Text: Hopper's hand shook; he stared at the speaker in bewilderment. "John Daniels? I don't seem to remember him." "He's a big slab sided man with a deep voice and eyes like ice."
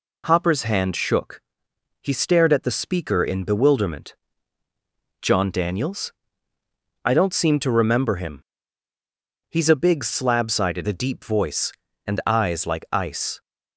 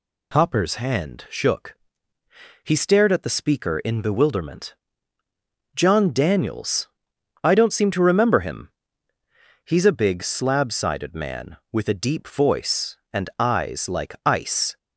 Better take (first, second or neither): second